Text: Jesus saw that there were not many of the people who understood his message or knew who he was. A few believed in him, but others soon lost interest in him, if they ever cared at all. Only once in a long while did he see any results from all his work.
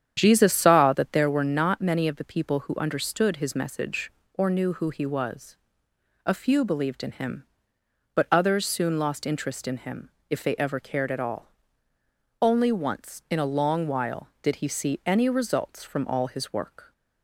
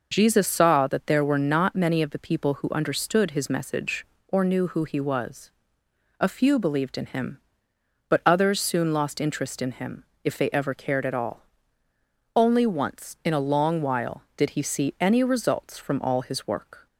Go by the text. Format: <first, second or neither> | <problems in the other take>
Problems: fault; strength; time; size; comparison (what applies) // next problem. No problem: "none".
second | starts louder than the rest; strong; until 1.4 s; 9 dB